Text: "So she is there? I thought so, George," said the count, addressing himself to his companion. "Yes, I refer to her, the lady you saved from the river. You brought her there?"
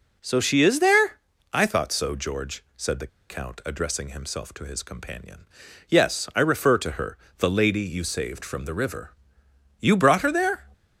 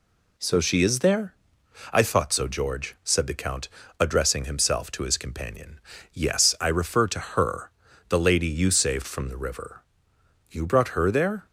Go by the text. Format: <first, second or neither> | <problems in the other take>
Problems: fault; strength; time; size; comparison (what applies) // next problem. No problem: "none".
second | pauses between "the" and "count"; slight; at 3.0 s; 0.21 s long